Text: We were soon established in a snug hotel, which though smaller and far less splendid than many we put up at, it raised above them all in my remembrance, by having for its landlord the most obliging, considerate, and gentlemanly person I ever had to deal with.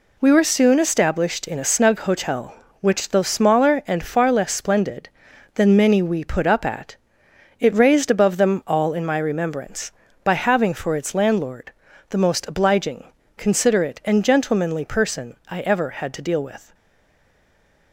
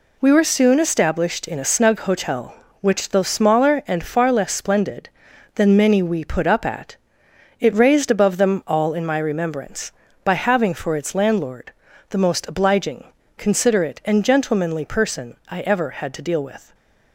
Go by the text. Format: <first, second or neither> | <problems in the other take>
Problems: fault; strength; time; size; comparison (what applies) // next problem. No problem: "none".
second | pauses between "landlord" and "the"; at 11.7 s; 0.38 s long; also in the second // stays silent after the last word; noticeable; from 16.7 s on; 1.2 s long